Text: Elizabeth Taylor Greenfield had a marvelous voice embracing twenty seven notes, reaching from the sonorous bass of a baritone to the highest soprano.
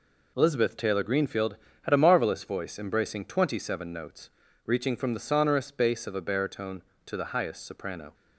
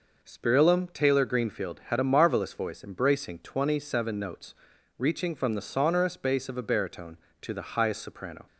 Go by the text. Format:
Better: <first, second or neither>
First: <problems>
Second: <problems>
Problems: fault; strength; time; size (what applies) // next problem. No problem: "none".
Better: first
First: none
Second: says "Spirillum" for "Elizabeth"; at 0.2 s